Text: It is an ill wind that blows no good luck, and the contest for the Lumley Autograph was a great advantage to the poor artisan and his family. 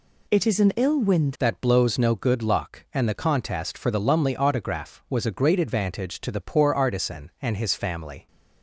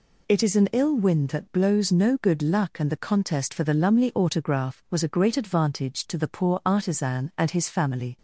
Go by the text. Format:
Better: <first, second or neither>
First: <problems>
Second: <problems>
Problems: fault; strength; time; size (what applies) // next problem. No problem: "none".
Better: second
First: changes voice at "that"; from 1.3 s on; 6.9 s long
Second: none